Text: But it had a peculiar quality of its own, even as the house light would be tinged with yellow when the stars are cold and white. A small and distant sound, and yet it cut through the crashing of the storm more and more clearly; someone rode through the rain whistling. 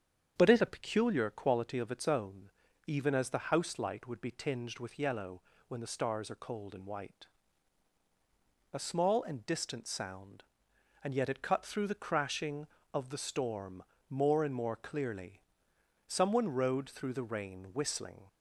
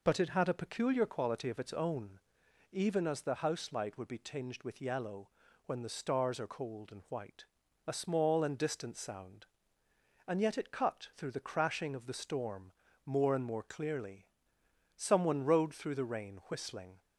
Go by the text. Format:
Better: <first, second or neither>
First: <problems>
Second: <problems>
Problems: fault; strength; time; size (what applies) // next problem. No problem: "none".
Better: second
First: starts louder than the rest; strong; until 1.3 s; 8 dB // skips "had"; at 0.6 s // pauses between "yellow" and "when"; slight; at 5.4 s; 0.28 s long // pauses between "storm" and "more"; slight; at 13.8 s; 0.28 s long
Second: pauses between "yellow" and "when"; at 5.2 s; 0.38 s long // pauses between "storm" and "more"; slight; at 12.7 s; 0.32 s long